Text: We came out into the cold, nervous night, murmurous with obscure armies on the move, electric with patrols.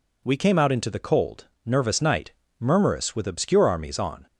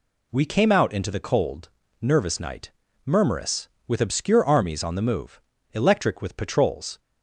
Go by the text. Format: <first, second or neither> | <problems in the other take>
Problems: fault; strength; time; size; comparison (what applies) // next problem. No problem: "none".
second | stops before "the move electric with patrols"; at 4.2 s